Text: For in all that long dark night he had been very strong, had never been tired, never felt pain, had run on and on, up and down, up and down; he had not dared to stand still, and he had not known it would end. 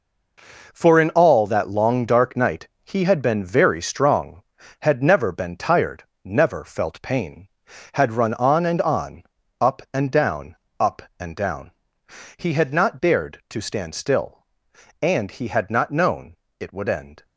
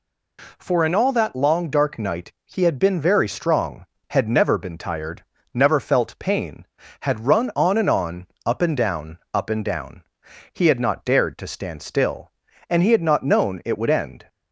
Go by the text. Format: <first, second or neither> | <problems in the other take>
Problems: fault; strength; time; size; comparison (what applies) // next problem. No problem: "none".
second | gets quieter; strong; throughout; 10 dB // pauses between "night" and "he"; slight; at 2.6 s; 0.16 s long // pauses between "known" and "it"; slight; at 16.3 s; 0.24 s long